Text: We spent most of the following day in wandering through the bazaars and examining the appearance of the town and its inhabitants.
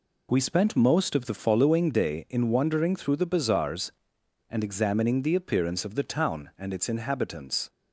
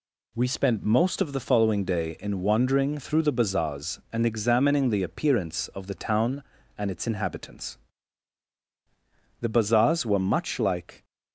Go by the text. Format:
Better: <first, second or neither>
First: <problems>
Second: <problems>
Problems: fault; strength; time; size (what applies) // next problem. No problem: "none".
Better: first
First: none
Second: goes on to say "The bazaars were much like"; from 9.4 s on; 1.6 s long